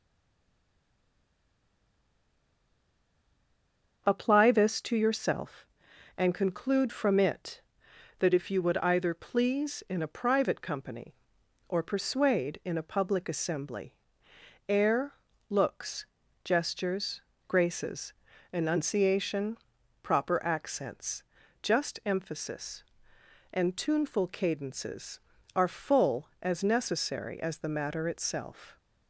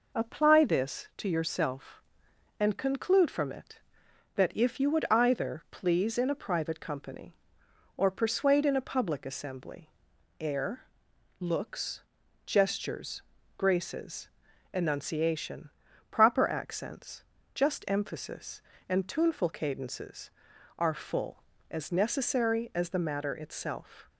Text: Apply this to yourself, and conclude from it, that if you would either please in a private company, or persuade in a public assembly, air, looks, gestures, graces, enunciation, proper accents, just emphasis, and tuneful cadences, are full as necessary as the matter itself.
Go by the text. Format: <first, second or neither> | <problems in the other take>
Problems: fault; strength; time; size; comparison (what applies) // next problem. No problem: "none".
second | stays silent before the first word; strong; until 4.0 s; 4.0 s long // starts louder than the rest; until 5.0 s; 6.5 dB